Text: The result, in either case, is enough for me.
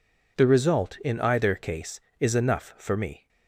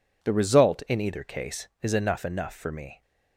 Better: first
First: none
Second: says "enough" twice; at 2.2 s

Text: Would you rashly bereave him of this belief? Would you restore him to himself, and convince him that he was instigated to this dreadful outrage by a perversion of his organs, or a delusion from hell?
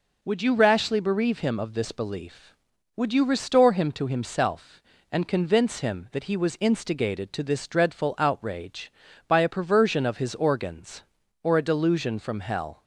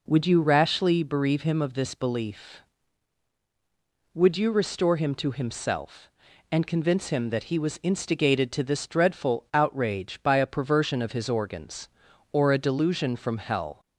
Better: neither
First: none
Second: none

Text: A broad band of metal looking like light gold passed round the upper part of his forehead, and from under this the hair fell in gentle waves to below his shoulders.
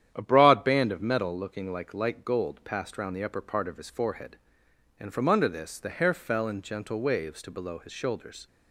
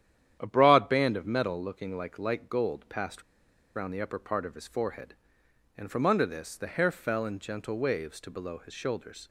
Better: first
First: starts louder than the rest; strong; until 1.1 s; 10 dB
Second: starts louder than the rest; strong; until 1.4 s; 10 dB // pauses between "passed" and "round"; noticeable; at 3.2 s; 0.53 s long

